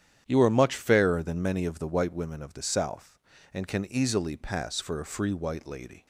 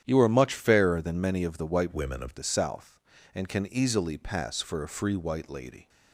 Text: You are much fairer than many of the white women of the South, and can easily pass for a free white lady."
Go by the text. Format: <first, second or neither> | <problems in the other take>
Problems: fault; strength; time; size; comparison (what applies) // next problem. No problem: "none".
first | starts louder than the rest; strong; until 1.0 s; 9.5 dB; strong in the first // changes voice from "women" to "of"; from 1.9 to 2.3 s; 0.4 s long